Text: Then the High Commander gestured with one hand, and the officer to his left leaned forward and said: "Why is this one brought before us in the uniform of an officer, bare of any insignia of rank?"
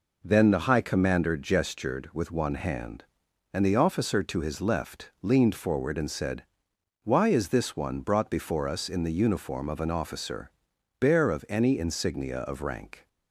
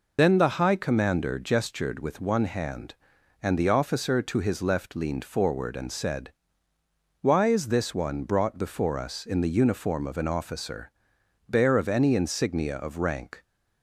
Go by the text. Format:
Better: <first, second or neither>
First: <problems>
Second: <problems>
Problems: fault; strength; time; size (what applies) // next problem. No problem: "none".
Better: first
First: none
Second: loses the start of "Then"; at 0.1 s; 75 ms